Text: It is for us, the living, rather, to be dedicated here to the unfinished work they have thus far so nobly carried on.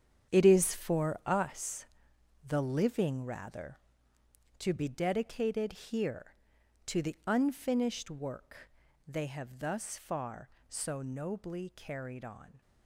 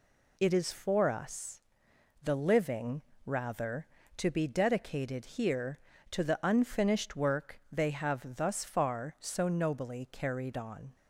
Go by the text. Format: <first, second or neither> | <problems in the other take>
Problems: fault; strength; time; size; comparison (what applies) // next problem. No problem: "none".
second | gets quieter; strong; throughout; 12 dB // pauses between "work" and "they"; slight; at 8.7 s; 0.36 s long